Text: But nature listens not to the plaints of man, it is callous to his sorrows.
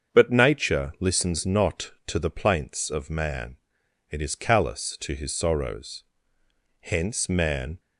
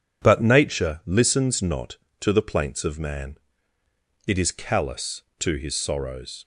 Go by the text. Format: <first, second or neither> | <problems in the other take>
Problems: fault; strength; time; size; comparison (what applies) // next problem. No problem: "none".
second | starts louder than the rest; until 1.2 s; 7 dB // goes on to say "Hence man"; noticeable; from 6.7 s on; 1.0 s long